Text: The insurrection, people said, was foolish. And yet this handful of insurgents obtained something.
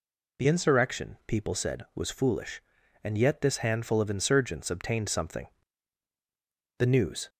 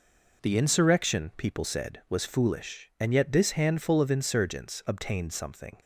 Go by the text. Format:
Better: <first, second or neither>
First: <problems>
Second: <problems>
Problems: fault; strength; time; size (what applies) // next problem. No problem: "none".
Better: second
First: goes on to say "The news"; from 6.7 s on; 0.50 s long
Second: none